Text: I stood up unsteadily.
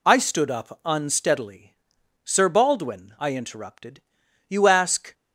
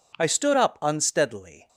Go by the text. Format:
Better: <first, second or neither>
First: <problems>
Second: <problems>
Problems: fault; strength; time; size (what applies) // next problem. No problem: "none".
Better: second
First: goes on to say "Sir Baldwin I interrupted you ask"; strong; from 2.2 s on; 2.8 s long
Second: none